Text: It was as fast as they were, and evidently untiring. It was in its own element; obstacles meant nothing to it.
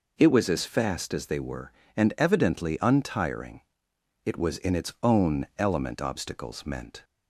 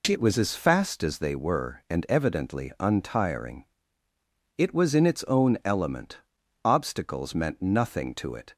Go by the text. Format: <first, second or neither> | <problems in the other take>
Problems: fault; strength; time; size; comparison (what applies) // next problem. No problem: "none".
second | stops before "nothing to it"; at 7.0 s